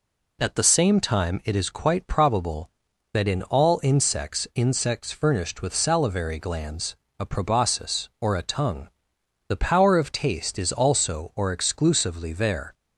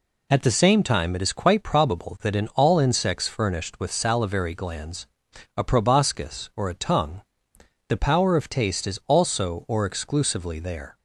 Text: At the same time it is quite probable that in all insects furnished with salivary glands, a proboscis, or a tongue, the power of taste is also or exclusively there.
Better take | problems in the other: second | says "insects" twice; at 4.5 s

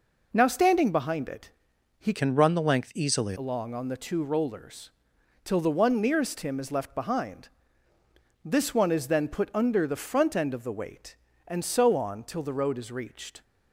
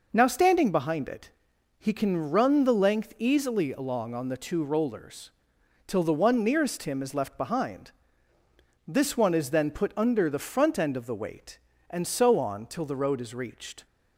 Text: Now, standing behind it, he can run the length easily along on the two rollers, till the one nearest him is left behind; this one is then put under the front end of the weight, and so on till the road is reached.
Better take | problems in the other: second | changes voice from "can" to "easily"; from 2.1 to 3.3 s; 1.2 s long

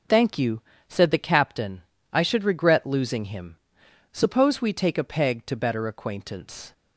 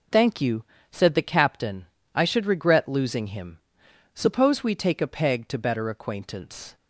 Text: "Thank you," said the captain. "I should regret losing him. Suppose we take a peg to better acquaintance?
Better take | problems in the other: neither | none

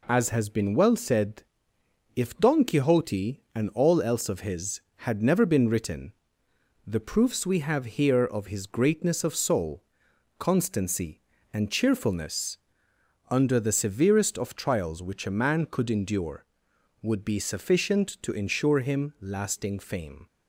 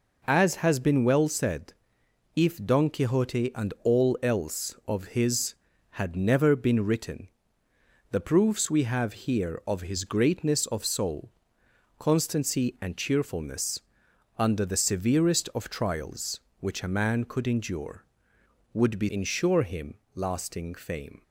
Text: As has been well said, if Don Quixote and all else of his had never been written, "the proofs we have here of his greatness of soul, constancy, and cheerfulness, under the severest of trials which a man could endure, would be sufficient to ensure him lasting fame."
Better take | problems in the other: first | skips "sufficient to"; at 19.0 s // pauses between "him" and "lasting"; slight; at 19.9 s; 0.20 s long

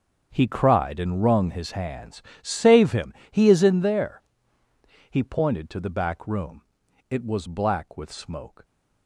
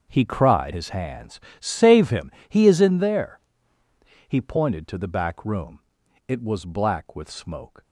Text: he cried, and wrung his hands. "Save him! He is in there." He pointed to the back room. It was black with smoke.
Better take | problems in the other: first | starts louder than the rest; until 1.0 s; 6.5 dB; also in the first // skips "and wrung"; at 0.7 s

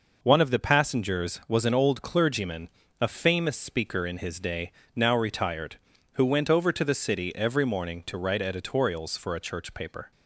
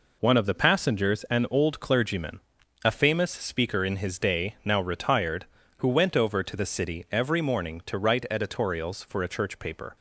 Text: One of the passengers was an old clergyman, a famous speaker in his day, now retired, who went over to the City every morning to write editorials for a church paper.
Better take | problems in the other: first | skips "was"; at 1.2 s

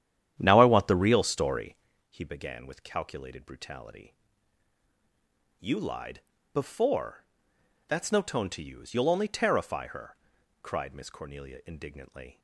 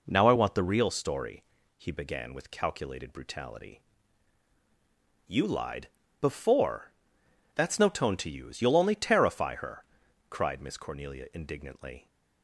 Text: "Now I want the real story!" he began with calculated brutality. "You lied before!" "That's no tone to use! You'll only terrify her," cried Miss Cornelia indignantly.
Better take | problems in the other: second | starts louder than the rest; strong; until 1.9 s; 10.5 dB // pauses between "lied" and "before"; slight; at 6.2 s; 0.32 s long; slight in the second

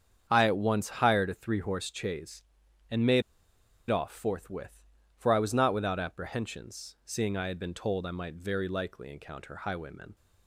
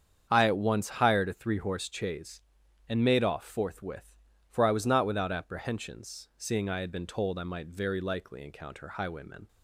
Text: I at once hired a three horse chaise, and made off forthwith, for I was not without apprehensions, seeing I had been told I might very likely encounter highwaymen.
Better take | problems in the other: second | starts louder than the rest; strong; until 1.3 s; 8 dB; strong in the second // pauses between "made" and "off"; noticeable; at 3.2 s; 0.66 s long

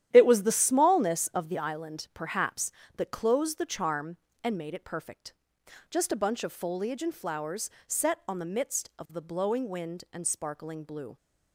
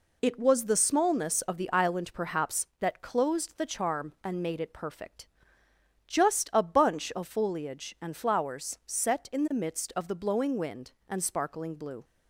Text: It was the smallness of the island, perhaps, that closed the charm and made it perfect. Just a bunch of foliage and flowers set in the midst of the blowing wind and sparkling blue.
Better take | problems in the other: second | starts louder than the rest; strong; until 1.1 s; 11 dB // pauses between "flowers" and "set"; slight; at 7.7 s; 0.16 s long // says "on" for "in"; at 8.2 s

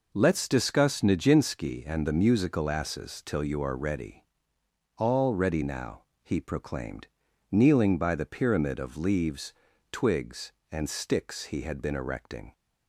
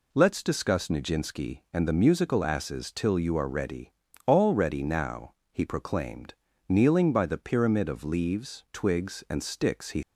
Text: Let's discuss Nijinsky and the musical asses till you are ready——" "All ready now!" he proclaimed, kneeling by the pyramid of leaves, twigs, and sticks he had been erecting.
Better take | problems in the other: first | stops before "had been erecting"; at 10.0 s

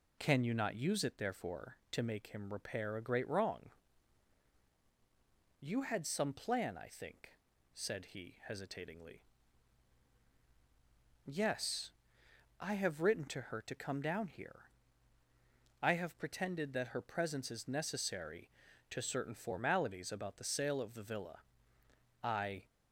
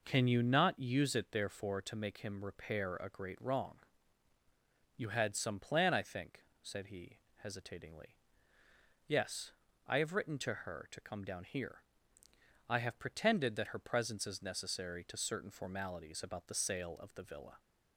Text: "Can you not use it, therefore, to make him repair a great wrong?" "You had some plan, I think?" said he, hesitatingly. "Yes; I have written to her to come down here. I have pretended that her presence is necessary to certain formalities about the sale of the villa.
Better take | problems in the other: second | goes on to say "I"; slight; from 22.2 s on; 0.40 s long

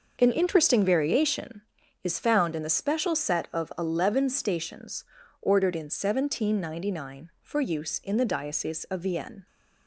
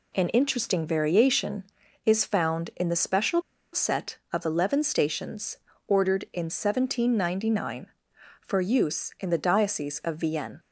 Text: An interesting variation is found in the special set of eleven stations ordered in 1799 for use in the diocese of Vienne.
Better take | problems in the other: first | pauses between "special" and "set"; slight; at 3.4 s; 0.31 s long // pauses between "stations" and "ordered"; slight; at 5.5 s; 0.32 s long; slight in the first

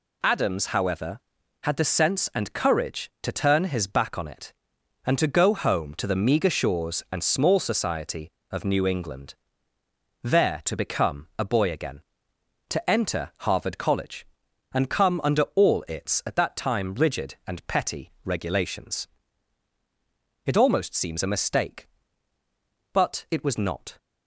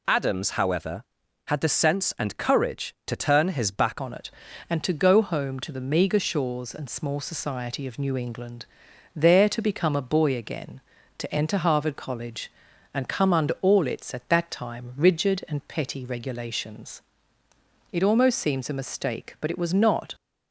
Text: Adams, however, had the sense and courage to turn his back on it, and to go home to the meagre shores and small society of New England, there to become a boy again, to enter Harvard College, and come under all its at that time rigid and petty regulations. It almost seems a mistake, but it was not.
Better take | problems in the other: first | changes voice at "on"; from 4.0 s on; 16.1 s long

